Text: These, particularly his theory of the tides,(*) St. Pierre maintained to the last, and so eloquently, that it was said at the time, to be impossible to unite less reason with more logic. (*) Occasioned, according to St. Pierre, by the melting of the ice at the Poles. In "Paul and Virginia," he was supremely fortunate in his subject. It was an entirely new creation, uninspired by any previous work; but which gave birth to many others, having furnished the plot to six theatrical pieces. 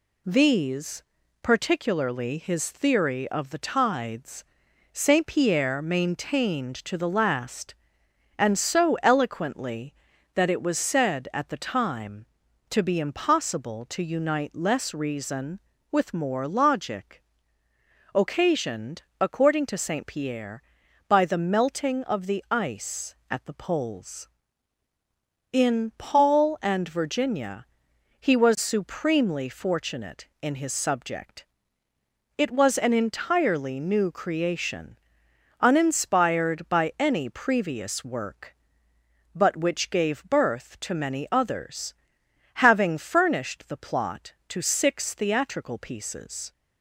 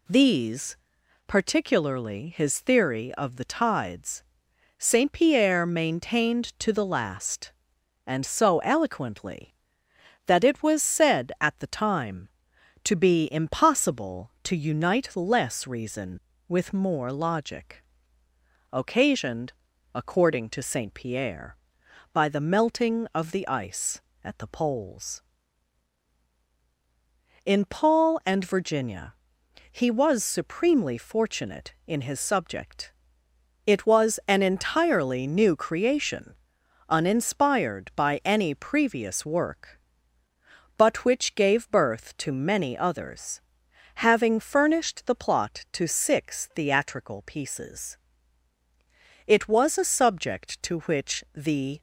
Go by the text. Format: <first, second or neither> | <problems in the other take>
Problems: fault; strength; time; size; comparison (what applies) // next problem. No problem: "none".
first | goes on to say "It was a subject to which the"; strong; from 49.2 s on; 2.5 s long